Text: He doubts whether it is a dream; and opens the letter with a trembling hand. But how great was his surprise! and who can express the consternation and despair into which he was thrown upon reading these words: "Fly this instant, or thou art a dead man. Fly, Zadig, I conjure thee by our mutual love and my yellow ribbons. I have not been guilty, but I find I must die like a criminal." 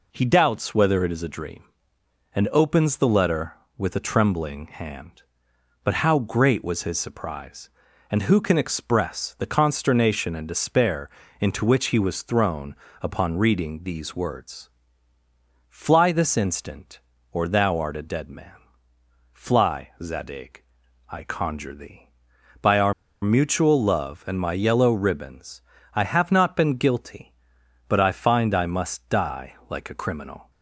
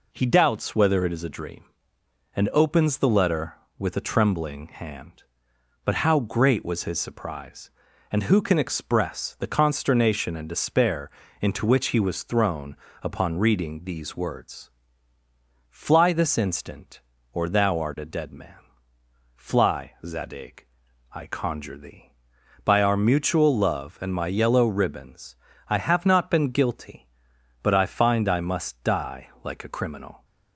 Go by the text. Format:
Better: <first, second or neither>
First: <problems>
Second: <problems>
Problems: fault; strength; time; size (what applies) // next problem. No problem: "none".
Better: second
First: pauses between "despair" and "into"; slight; at 11.0 s; 0.30 s long // pauses between "thrown" and "upon"; slight; at 12.7 s; 0.26 s long // pauses between "our" and "mutual"; slight; at 22.9 s; 0.29 s long // pauses between "die" and "like"; slight; at 29.5 s; 0.16 s long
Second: pauses between "despair" and "into"; slight; at 11.1 s; 0.30 s long // pauses between "thrown" and "upon"; slight; at 12.7 s; 0.26 s long // pauses between "die" and "like"; slight; at 29.2 s; 0.16 s long